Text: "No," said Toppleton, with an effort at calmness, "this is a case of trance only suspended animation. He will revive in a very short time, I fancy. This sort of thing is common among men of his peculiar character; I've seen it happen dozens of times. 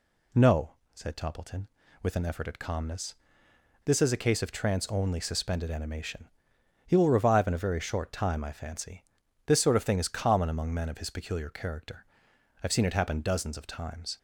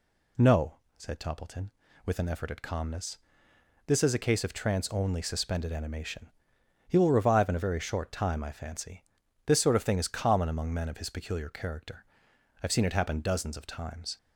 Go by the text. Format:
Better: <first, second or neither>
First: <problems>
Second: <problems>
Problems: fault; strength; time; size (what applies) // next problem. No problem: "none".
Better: neither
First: none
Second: none